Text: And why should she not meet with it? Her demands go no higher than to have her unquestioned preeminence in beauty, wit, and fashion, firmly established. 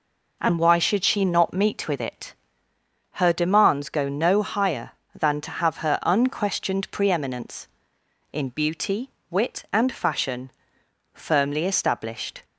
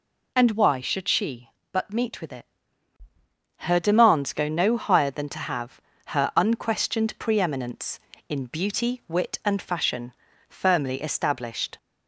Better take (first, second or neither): first